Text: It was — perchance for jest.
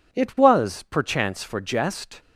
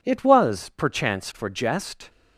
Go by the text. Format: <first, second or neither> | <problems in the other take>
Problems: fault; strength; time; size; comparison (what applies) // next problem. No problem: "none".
neither | none